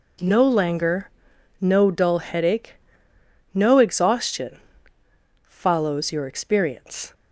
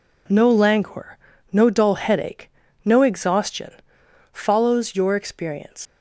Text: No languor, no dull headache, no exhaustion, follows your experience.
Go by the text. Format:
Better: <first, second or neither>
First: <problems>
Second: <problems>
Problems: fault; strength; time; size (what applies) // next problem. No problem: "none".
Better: first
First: none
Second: leaves "experience" unfinished; at 5.8 s; 75 ms